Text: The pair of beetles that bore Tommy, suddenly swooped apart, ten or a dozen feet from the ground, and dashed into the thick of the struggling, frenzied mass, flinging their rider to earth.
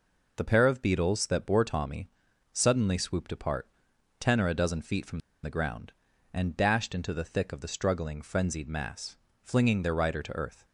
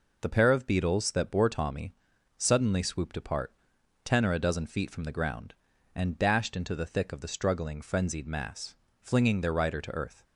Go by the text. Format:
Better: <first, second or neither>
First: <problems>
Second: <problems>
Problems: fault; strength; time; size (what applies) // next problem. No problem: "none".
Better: second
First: pauses between "from" and "the"; slight; at 5.1 s; 0.23 s long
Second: none